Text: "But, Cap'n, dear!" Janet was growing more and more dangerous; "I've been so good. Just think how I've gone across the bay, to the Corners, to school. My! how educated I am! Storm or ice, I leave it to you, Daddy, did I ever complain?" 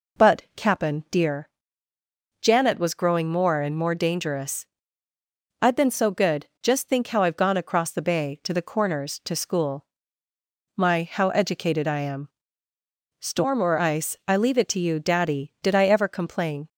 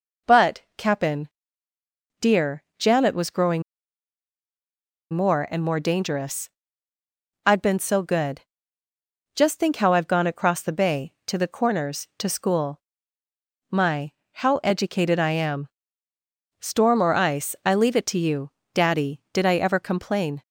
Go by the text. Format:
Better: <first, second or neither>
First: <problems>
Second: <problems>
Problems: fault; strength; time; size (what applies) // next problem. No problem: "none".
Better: first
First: none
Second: pauses between "growing" and "more"; strong; at 3.6 s; 1.5 s long